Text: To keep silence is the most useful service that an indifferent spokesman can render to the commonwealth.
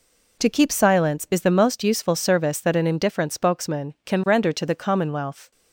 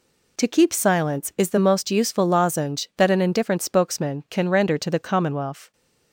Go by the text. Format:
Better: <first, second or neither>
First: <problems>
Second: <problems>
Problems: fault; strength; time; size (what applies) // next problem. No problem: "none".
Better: first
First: none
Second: says "lozenge" for "service"; at 2.2 s